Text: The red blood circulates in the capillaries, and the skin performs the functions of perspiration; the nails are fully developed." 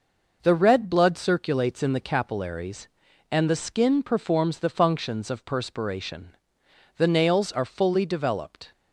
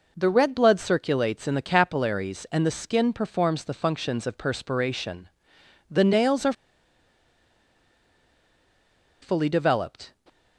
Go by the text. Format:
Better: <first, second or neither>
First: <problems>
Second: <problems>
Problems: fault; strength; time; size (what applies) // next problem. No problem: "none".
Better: first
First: none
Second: pauses between "are" and "fully"; strong; at 6.5 s; 2.6 s long